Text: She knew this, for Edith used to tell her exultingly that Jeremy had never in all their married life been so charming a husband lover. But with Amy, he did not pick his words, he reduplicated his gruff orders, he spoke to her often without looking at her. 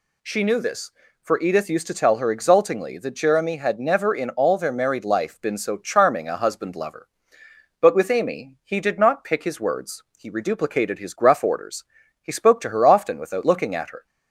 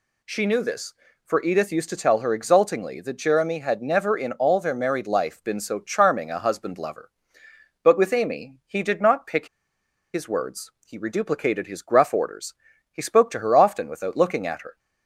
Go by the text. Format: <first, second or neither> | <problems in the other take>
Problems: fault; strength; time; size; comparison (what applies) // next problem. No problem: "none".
first | pauses between "pick" and "his"; noticeable; at 9.4 s; 0.67 s long